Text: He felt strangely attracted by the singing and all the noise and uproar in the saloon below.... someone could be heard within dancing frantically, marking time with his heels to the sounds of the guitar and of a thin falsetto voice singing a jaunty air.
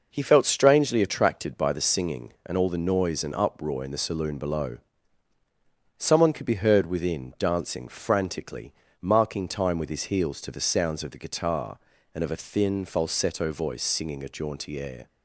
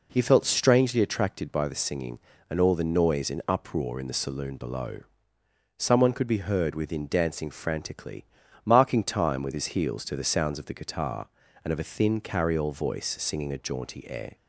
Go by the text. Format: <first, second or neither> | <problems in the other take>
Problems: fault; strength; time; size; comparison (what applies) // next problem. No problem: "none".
first | says "carryall" for "falsetto"; at 12.1 s